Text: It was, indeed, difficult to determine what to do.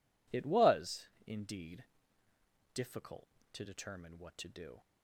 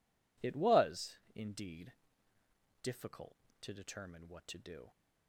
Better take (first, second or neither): neither